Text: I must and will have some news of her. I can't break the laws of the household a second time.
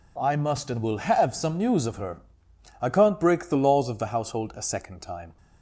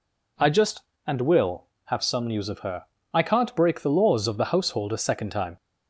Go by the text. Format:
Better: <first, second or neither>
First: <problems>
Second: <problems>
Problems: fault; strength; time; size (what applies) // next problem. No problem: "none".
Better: first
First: none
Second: says "just" for "must"; at 0.5 s